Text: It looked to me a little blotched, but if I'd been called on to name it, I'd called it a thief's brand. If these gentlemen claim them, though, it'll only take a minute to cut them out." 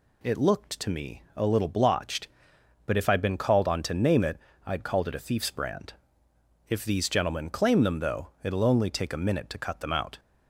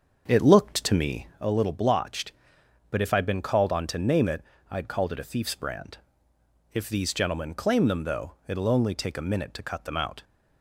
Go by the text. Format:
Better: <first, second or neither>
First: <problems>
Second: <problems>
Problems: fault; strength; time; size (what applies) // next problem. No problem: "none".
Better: first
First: none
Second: starts louder than the rest; until 1.5 s; 6.5 dB